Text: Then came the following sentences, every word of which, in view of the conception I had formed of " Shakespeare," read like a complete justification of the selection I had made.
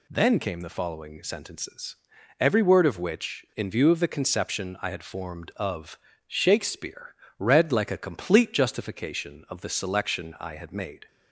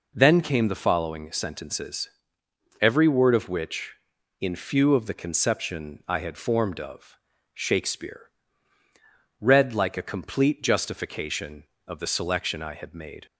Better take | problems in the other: first | says "few" for "view"; at 4.5 s

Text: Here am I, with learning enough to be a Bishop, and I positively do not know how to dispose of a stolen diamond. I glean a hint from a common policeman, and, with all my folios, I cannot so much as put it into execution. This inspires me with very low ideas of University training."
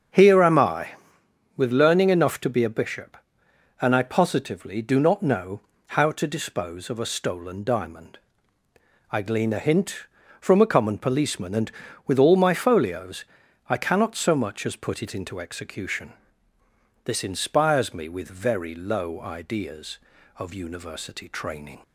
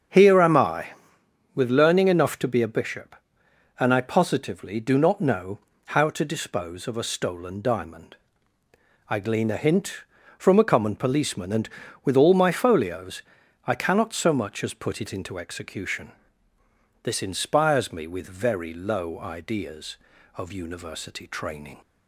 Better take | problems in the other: neither | starts louder than the rest; strong; the same in both // pauses between "know" and "how"; slight; the same in both

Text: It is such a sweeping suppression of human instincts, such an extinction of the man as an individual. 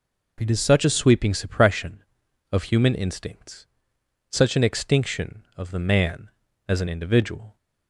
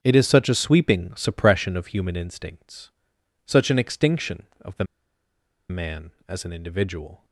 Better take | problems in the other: first | starts louder than the rest; strong; until 1.0 s; 8 dB // pauses between "the" and "man"; noticeable; at 4.8 s; 0.84 s long

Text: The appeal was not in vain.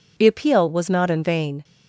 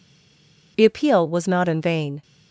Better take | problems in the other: first | stays silent before the first word; slight; until 0.7 s; 0.7 s long

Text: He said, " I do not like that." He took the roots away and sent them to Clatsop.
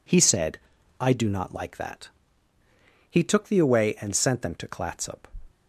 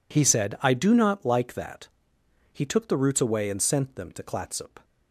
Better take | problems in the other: second | skips "roots"; at 3.5 s

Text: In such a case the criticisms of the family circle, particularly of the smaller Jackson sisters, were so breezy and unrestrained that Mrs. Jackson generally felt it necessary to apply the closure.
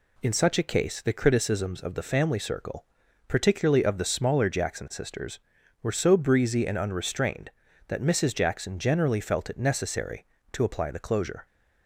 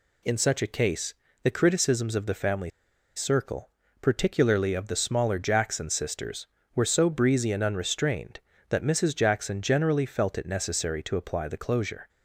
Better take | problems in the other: first | pauses between "case" and "the"; slight; at 1.1 s; 0.28 s long // pauses between "family" and "circle"; noticeable; at 2.6 s; 0.47 s long

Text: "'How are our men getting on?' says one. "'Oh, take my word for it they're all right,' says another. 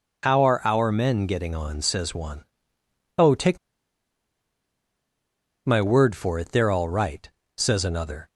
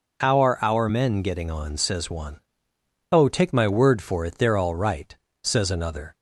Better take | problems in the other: second | pauses between "take" and "my"; strong; at 3.5 s; 2.0 s long

